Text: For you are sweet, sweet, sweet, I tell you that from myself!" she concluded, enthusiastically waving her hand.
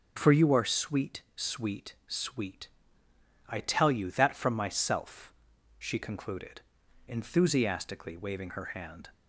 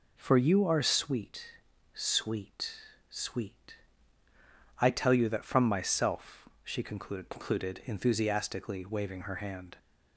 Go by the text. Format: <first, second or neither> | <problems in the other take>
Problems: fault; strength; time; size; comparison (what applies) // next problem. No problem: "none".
first | says "concluded" twice; at 7.2 s